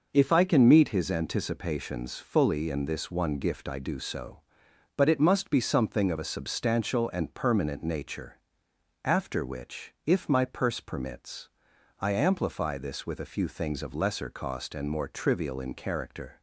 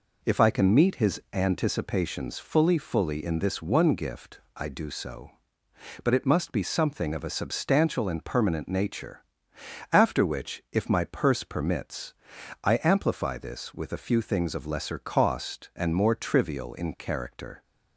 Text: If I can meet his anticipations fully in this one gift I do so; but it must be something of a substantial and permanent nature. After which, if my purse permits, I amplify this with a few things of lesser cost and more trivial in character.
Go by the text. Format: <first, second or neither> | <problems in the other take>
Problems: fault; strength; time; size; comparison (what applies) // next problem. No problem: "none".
first | says "fully" twice; at 2.7 s // pauses between "gift" and "I"; slight; at 4.3 s; 0.16 s long